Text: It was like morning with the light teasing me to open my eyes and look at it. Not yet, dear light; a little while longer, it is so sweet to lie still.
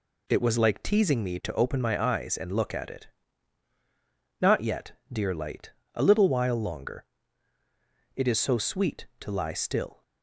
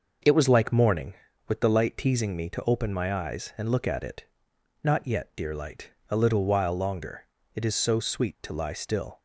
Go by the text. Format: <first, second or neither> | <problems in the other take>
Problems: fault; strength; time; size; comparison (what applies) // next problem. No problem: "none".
second | skips "morning with the light"; at 0.8 s